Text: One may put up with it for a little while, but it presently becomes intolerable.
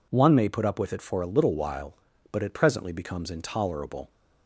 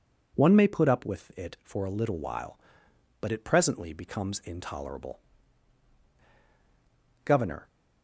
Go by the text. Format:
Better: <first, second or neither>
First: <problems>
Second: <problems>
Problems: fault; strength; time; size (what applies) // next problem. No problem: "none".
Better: first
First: none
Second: goes on to say "Governor"; slight; from 7.2 s on; 0.44 s long